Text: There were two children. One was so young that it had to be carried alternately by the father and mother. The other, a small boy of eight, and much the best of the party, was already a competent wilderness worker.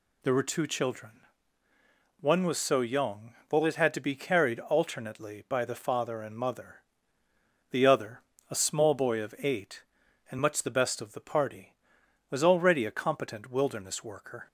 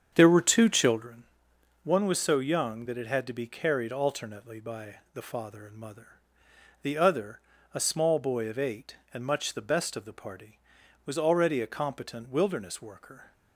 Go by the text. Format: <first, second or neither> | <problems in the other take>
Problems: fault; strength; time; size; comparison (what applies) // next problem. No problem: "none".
first | starts louder than the rest; strong; until 1.0 s; 7.5 dB // pauses between "by" and "the"; slight; at 4.9 s; 0.18 s long